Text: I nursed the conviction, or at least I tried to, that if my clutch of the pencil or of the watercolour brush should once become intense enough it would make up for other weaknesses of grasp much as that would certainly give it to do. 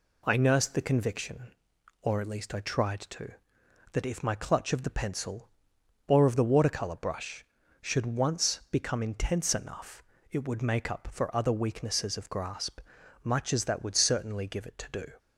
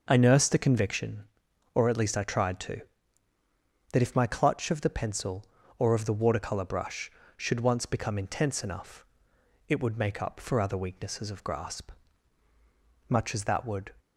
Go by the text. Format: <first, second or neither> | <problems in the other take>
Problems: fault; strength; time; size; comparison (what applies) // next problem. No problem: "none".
first | pauses between "enough" and "it"; noticeable; at 9.0 s; 0.62 s long; slight in the first // pauses between "grasp" and "much"; at 11.9 s; 1.1 s long; also in the first // stops before "certainly give it to do"; at 13.9 s